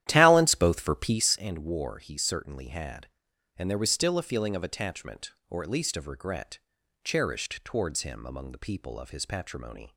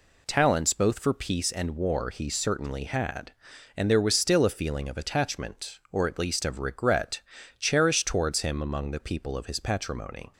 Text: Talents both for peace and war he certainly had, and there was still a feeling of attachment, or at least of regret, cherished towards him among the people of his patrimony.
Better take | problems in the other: second | starts louder than the rest; strong; until 1.5 s; 12 dB

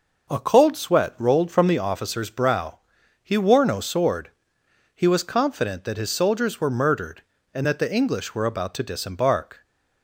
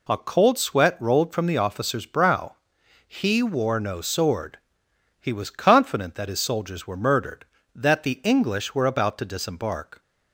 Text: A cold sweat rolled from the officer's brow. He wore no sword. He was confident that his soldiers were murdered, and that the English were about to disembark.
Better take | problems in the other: first | skips "and"; at 7.5 s

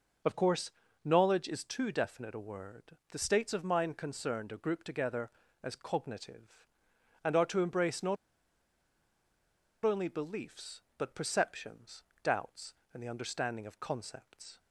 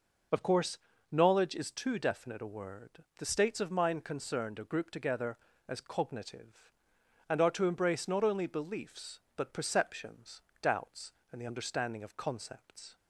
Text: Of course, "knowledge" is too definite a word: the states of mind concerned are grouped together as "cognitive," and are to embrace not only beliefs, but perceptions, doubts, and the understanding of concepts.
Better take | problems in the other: second | pauses between "not" and "only"; strong; at 8.1 s; 1.6 s long

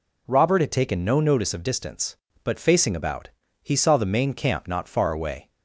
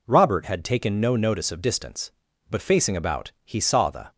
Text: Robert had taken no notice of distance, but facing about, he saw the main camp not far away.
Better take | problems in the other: first | stops before "main camp not far away"; at 4.1 s

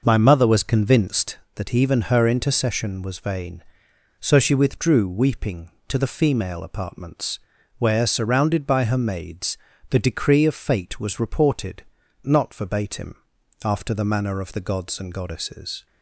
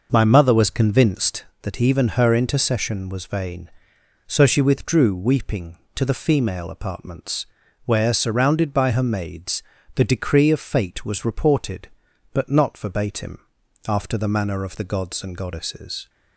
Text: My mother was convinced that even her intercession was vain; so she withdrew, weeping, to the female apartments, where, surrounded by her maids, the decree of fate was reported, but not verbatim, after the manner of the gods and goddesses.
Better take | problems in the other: second | skips "but"; at 12.0 s

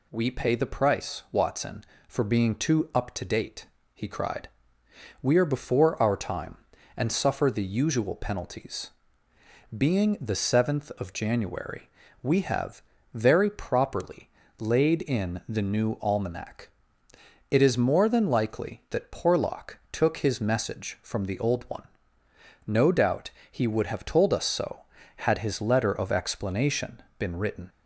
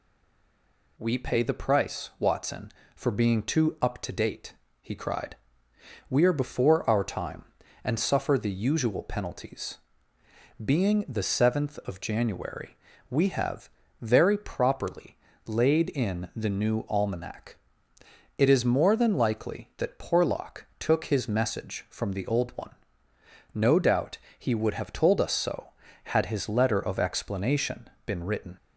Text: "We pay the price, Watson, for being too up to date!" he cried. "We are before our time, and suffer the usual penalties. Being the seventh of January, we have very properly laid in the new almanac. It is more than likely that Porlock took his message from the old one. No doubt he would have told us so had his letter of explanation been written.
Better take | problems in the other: first | stays silent before the first word; until 0.9 s; 0.9 s long // pauses between "have" and "very"; slight; at 13.6 s; 0.32 s long; slight in the first // pauses between "properly" and "laid"; slight; at 15.1 s; 0.28 s long; slight in the first // pauses between "doubt" and "he"; slight; at 24.1 s; 0.22 s long; slight in the first // pauses between "explanation" and "been"; slight; at 27.9 s; 0.16 s long; slight in the first

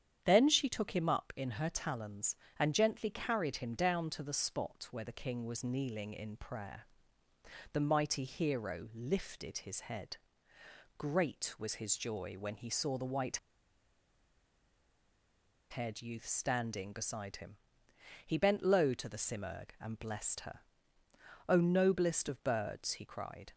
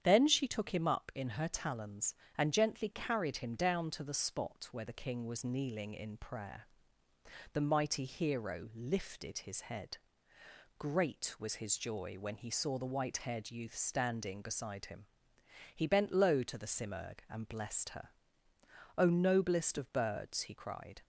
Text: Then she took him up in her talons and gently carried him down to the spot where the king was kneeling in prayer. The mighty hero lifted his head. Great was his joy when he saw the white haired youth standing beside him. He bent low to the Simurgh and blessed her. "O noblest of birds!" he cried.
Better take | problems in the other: second | starts louder than the rest; strong; until 1.2 s; 9 dB; strong in the second // pauses between "white" and "haired"; strong; at 13.3 s; 2.3 s long

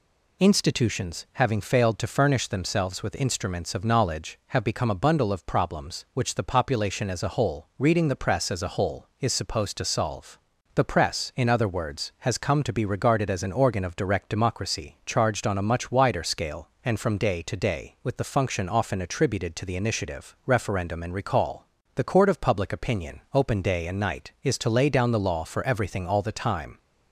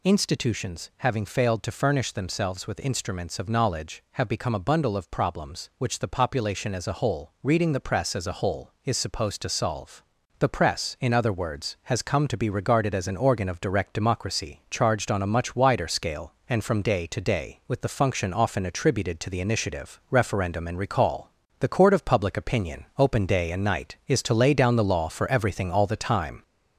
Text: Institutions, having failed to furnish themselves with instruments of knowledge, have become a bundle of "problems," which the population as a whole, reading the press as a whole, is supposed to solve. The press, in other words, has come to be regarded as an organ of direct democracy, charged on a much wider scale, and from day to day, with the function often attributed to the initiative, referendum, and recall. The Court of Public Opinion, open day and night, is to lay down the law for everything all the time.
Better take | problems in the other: first | gets louder; slight; throughout; 3.5 dB

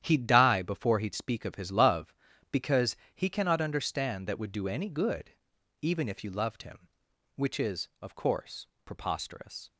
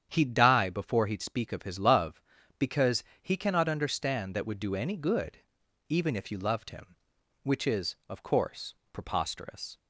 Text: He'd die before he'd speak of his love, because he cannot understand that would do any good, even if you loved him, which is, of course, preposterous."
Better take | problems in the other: second | gets quieter; strong; throughout; 10.5 dB // starts louder than the rest; strong; until 1.0 s; 10.5 dB; strong in the second // pauses between "because" and "he"; slight; at 2.9 s; 0.18 s long; slight in the second

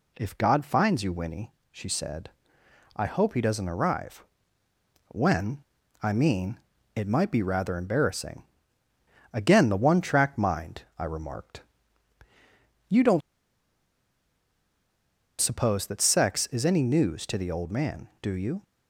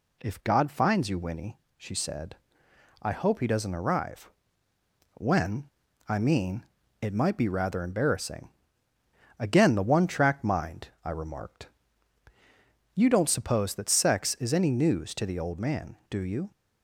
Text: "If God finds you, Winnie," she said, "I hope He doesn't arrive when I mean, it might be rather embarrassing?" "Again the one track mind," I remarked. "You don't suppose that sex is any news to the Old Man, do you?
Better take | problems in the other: second | pauses between "arrive" and "when"; noticeable; at 4.2 s; 0.86 s long; noticeable in the second // pauses between "when" and "I"; at 5.6 s; 0.38 s long; also in the second // pauses between "don't" and "suppose"; strong; at 13.2 s; 2.2 s long

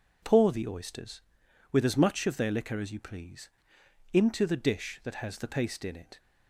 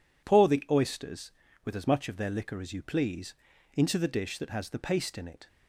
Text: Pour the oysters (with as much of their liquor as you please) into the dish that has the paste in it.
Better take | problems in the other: neither | none

